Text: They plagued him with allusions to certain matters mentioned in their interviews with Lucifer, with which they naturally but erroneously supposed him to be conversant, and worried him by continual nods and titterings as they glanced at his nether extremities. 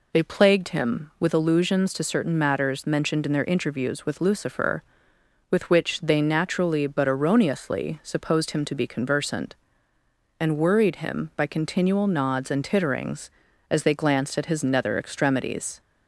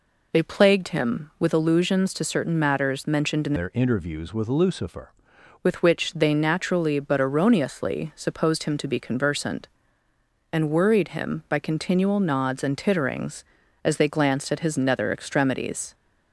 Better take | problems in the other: first | changes voice from "their" to "Lucifer"; from 3.5 to 5.1 s; 1.6 s long

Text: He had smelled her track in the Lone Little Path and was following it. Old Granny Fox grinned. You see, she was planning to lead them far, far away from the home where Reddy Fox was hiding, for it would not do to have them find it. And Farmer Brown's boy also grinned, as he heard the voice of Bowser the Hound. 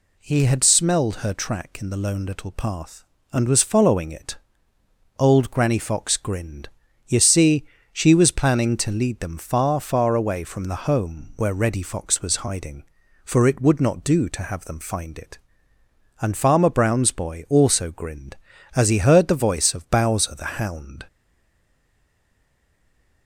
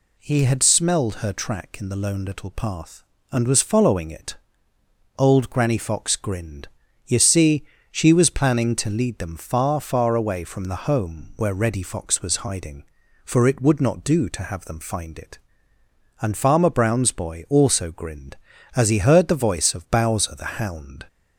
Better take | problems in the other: second | stays silent after the last word; from 21.0 s on; 2.2 s long

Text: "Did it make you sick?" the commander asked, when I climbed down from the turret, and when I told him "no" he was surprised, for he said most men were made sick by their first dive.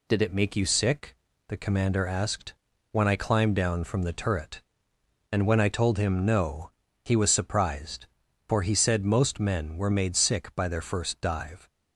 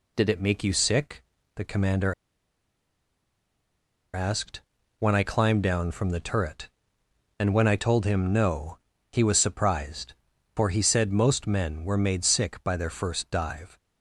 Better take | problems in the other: first | pauses between "commander" and "asked"; strong; at 2.1 s; 2.0 s long // pauses between "no" and "he"; slight; at 8.7 s; 0.34 s long; slight in the first

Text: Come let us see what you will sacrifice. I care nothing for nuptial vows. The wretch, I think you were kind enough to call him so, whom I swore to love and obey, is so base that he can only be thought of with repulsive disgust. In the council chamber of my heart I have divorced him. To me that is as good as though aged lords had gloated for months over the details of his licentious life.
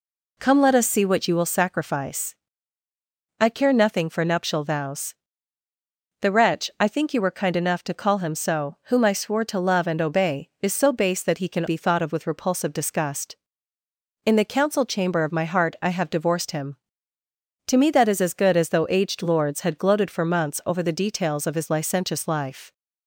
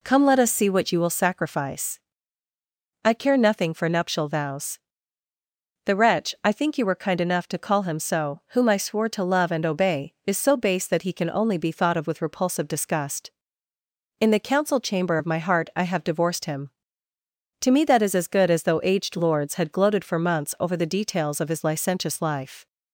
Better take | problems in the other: second | skips "only"; at 11.6 s

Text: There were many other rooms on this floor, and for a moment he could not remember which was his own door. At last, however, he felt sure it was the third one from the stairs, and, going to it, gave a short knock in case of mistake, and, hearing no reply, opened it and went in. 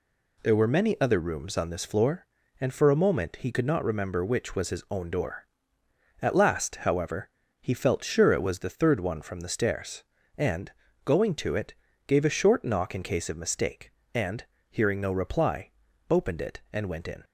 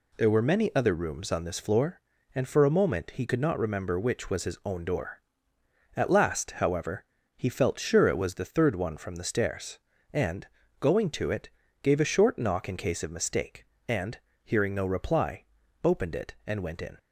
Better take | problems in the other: neither | none

